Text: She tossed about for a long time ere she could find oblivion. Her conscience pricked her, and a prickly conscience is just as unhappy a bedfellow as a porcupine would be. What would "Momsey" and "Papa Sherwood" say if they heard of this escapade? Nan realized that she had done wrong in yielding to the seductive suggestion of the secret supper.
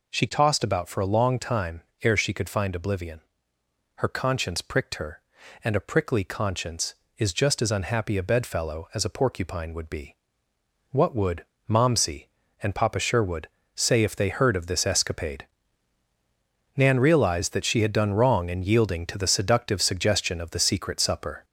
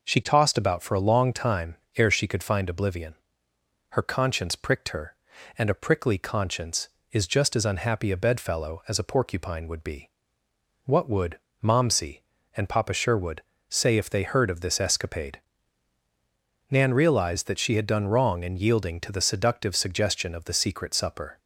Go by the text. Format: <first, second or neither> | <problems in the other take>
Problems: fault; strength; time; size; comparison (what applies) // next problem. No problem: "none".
second | gets louder; throughout; 3.5 dB // pauses between "time" and "ere"; slight; at 1.8 s; 0.20 s long; slight in the second // pauses between "would" and "Momsey"; slight; at 11.4 s; 0.24 s long; slight in the second // pauses between "Sherwood" and "say"; slight; at 13.4 s; 0.26 s long; slight in the second